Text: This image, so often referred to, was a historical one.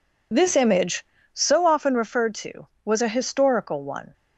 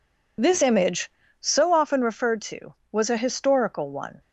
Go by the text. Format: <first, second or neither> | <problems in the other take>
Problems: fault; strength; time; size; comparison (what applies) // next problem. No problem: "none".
neither | none